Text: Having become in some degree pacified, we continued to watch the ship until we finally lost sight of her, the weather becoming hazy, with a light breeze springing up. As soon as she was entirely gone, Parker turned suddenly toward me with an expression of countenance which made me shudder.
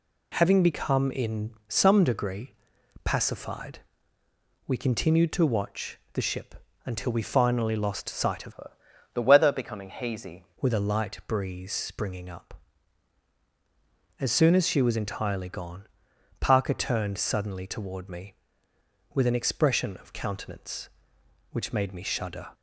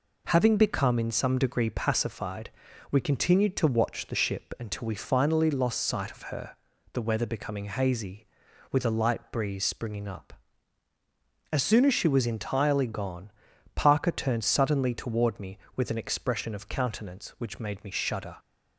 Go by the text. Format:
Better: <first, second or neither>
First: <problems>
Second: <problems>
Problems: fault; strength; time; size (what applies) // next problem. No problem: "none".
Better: second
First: pauses between "in" and "some"; slight; at 1.5 s; 0.18 s long // pauses between "degree" and "pacified"; noticeable; at 2.5 s; 0.50 s long // pauses between "watch" and "the"; slight; at 5.9 s; 0.16 s long // pauses between "ship" and "until"; slight; at 6.5 s; 0.32 s long // changes voice from "her" to "hazy"; from 8.5 to 10.4 s; 1.9 s long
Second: none